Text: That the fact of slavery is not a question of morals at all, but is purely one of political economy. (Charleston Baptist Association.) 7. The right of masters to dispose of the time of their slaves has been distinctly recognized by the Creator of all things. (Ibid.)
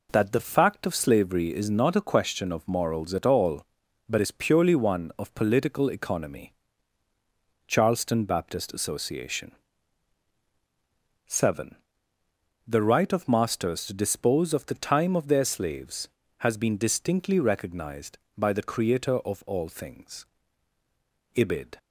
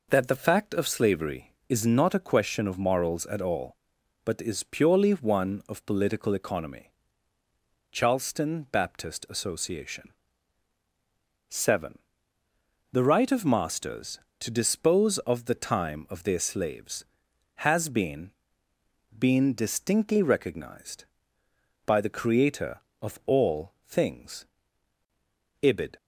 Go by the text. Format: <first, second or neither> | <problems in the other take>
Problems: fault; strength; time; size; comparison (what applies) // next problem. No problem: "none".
first | says "been" twice; at 19.1 s // pauses between "all" and "things"; slight; at 23.7 s; 0.16 s long